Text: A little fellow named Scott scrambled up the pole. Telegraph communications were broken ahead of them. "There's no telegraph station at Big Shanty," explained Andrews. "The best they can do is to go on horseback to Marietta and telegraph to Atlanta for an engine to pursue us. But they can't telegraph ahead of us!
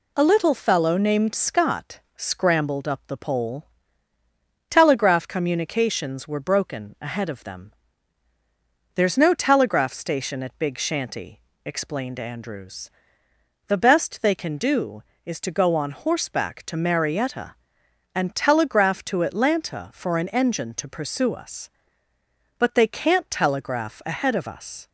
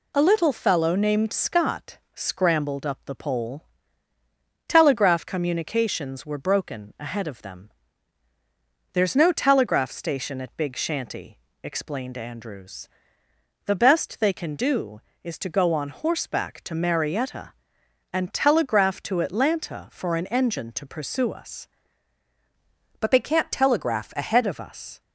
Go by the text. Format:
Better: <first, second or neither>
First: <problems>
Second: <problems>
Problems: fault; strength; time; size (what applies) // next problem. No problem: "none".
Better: first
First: pauses between "Scott" and "scrambled"; slight; at 2.0 s; 0.16 s long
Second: pauses between "Scott" and "scrambled"; slight; at 1.9 s; 0.16 s long // changes voice from "But" to "ahead"; from 22.9 to 24.4 s; 1.5 s long